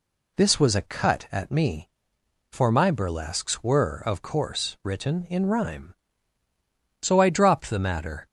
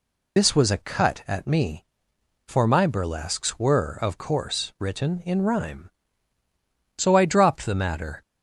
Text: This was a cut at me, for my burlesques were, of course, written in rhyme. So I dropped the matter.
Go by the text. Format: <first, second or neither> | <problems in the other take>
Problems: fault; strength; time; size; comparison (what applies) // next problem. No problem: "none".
first | loses the start of "This"; at 0.3 s; 50 ms